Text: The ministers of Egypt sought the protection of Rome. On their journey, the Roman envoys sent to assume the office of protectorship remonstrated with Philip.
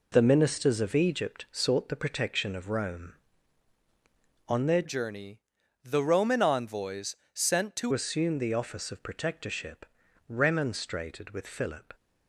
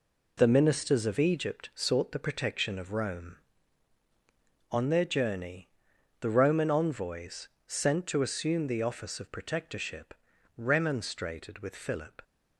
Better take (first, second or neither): second